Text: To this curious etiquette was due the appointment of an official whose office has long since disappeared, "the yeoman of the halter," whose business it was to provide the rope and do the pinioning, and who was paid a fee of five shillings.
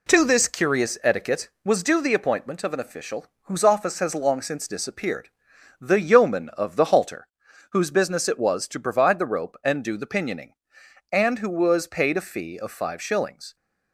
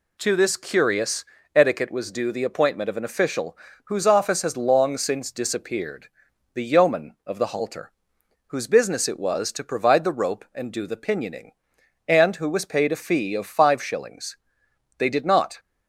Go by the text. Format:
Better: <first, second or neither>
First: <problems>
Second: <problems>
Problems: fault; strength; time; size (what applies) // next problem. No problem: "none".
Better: first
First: pauses between "official" and "whose"; slight; at 3.2 s; 0.18 s long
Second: pauses between "curious" and "etiquette"; slight; at 1.2 s; 0.28 s long // pauses between "official" and "whose"; slight; at 3.5 s; 0.28 s long // goes on to say "They did not"; from 14.9 s on; 0.60 s long